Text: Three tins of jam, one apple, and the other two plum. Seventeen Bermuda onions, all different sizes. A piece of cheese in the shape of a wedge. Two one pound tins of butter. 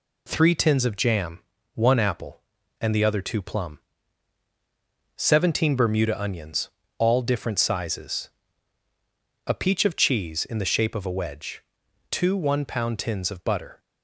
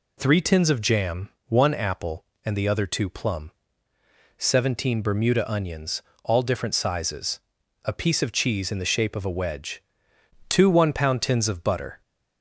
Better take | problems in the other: second | says "peach" for "piece"; at 9.5 s

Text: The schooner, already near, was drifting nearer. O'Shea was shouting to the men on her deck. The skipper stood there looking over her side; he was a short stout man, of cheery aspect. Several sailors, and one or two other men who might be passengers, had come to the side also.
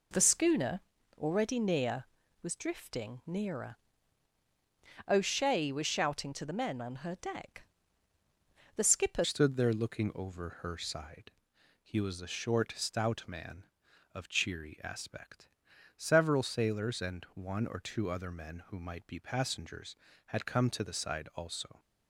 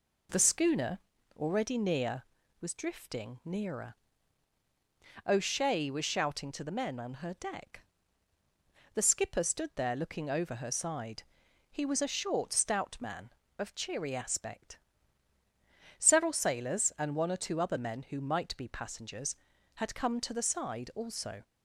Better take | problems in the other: second | changes voice at "stood"; from 9.2 s on; 12.5 s long

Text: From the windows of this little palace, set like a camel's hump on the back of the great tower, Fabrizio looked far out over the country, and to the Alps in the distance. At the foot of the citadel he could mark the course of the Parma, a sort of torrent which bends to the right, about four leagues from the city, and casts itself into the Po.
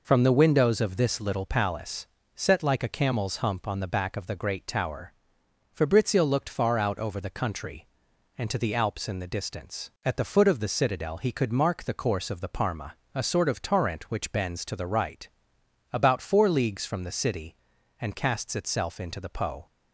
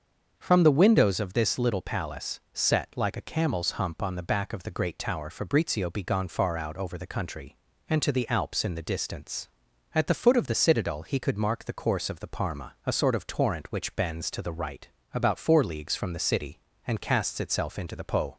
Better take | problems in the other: first | starts louder than the rest; until 1.3 s; 6.5 dB // says "begone" for "looked"; at 5.9 s

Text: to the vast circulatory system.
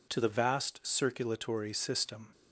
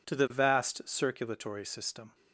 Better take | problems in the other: neither | none

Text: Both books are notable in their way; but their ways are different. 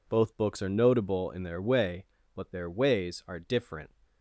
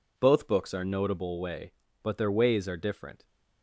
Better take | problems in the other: first | skips "in their"; at 1.4 s

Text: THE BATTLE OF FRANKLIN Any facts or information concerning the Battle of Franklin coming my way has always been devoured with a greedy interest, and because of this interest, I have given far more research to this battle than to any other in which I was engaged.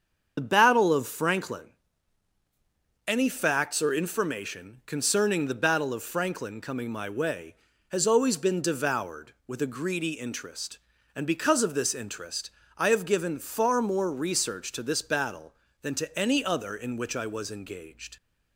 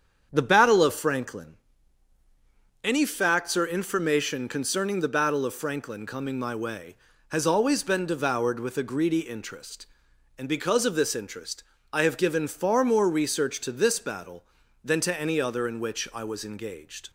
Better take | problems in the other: second | loses the start of "THE"; at 0.3 s; 30 ms // starts louder than the rest; strong; until 1.3 s; 7.5 dB; strong in the second // pauses between "FRANKLIN" and "Any"; strong; at 1.6 s; 1.4 s long; strong in the second

